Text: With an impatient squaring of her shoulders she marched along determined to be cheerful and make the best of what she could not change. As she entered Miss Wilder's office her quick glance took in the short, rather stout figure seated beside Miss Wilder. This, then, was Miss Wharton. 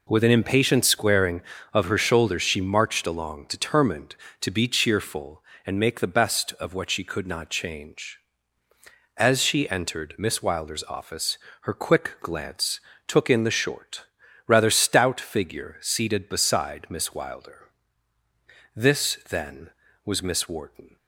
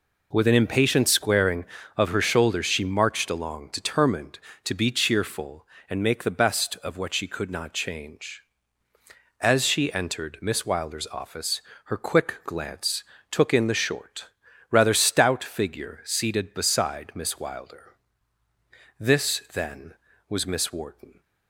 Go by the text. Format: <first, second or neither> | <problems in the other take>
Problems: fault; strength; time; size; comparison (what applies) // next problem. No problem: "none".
neither | pauses between "office" and "her"; slight; the same in both // pauses between "glance" and "took"; slight; the same in both